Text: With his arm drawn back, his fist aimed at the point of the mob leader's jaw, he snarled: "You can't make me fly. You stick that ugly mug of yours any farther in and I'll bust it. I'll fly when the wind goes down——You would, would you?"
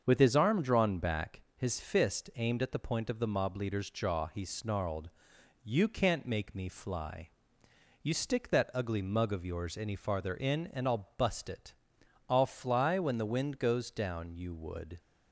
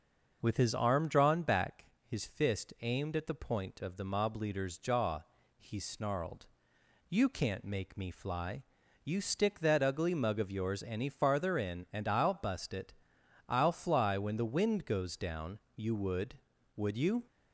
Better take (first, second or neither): second